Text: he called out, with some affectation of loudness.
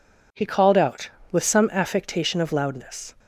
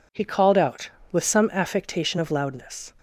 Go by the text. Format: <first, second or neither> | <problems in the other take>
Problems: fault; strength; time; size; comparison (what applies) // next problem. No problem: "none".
neither | none